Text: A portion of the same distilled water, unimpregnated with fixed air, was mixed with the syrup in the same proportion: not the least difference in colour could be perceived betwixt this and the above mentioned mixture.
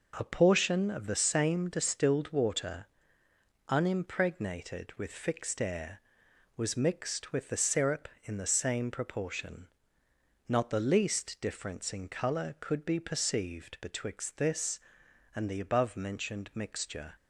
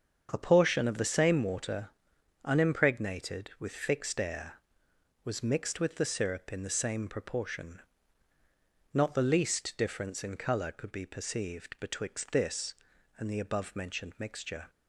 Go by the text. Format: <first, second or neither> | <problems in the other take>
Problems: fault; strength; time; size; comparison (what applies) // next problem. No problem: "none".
first | starts louder than the rest; strong; until 1.3 s; 7 dB // skips "distilled"; at 1.4 s